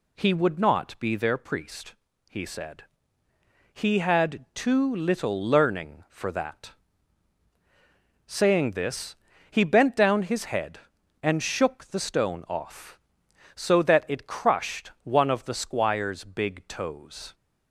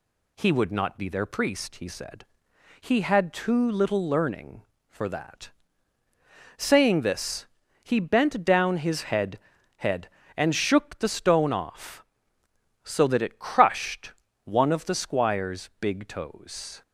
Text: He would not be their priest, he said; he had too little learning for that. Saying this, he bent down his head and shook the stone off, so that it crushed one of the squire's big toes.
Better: first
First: none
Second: says "head" twice; at 9.7 s // pauses between "crushed" and "one"; slight; at 14.1 s; 0.32 s long

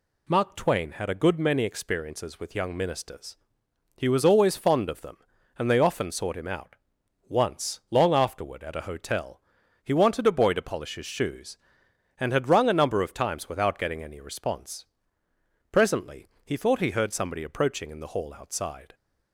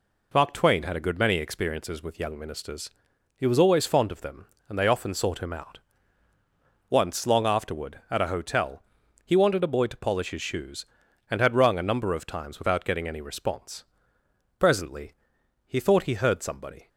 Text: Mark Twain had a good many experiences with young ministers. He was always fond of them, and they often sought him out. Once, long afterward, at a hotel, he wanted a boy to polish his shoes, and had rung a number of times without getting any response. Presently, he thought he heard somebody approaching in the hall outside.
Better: first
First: none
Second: stops before "approaching in the hall outside"; at 16.8 s

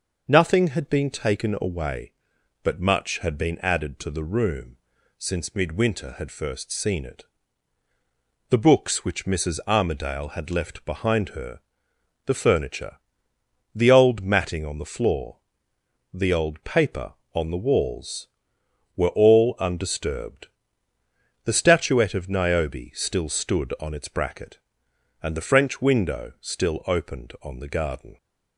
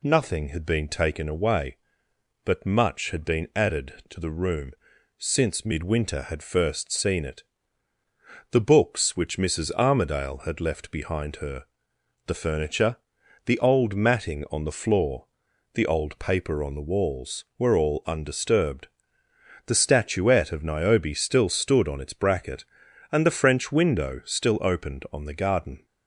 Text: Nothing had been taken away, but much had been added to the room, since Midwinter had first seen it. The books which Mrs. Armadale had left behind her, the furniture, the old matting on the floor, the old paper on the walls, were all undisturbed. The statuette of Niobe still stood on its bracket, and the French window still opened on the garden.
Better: neither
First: none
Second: none

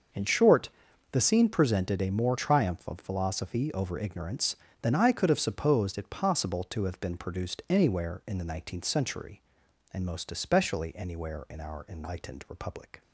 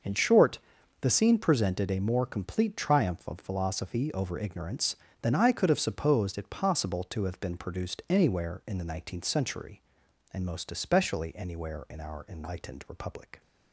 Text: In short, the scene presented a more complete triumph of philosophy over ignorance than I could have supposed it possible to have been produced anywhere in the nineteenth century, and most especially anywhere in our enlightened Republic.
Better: second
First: starts louder than the rest; until 1.5 s; 6 dB // skips "complete"; at 2.3 s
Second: starts louder than the rest; noticeable; until 1.4 s; 6 dB

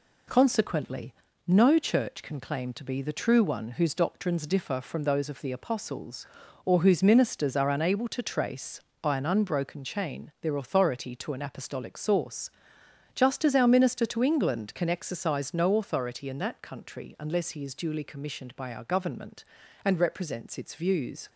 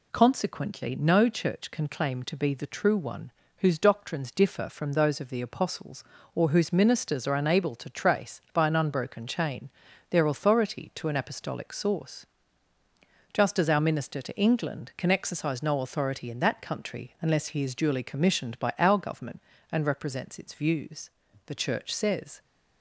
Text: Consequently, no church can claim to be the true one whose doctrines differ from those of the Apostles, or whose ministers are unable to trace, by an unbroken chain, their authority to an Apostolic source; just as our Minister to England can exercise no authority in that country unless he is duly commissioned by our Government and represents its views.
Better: first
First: none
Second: pauses between "one" and "whose"; slight; at 3.3 s; 0.26 s long // goes on to say "The Church says"; noticeable; from 21.4 s on; 0.96 s long

